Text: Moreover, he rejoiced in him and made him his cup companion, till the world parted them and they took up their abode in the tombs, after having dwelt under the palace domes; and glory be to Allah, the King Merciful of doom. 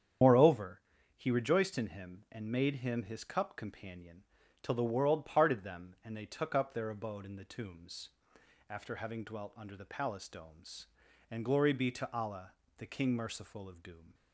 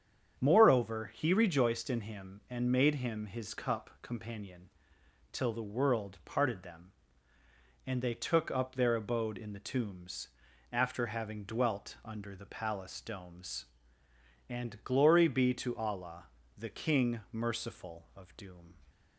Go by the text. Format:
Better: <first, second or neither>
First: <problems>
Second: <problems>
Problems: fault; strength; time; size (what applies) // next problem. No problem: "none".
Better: second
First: loses the start of "Moreover"; at 0.2 s; 75 ms // starts louder than the rest; strong; until 1.5 s; 8.5 dB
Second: starts louder than the rest; strong; until 1.4 s; 8 dB